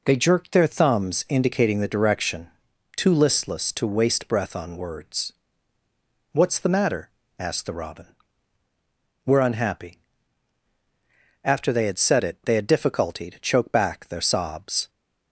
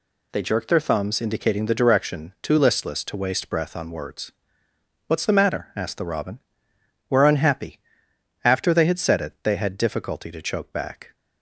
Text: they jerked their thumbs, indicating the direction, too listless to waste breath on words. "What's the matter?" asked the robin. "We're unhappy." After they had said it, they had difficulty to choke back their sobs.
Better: first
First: none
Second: stops before "their sobs"; at 11.1 s

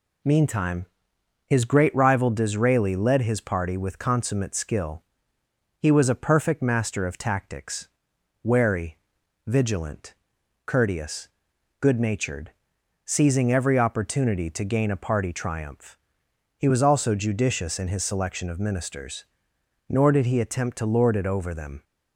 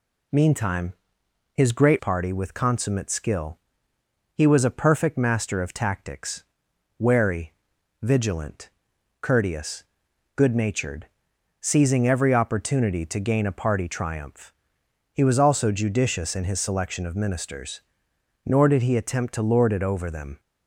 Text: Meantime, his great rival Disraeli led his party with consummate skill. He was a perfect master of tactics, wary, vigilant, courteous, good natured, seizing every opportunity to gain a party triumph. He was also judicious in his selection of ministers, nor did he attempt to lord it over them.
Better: first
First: none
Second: skips "rival Disraeli led his"; at 1.9 s

